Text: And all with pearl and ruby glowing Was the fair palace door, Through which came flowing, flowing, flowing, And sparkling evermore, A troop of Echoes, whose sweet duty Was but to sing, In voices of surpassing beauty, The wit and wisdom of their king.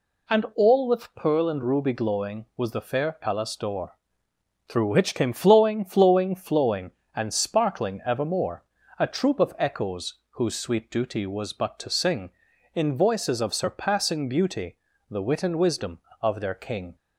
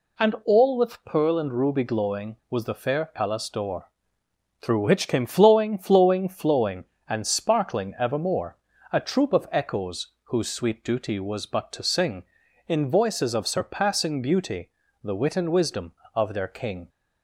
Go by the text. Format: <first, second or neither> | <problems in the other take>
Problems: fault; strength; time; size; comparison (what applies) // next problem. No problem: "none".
neither | none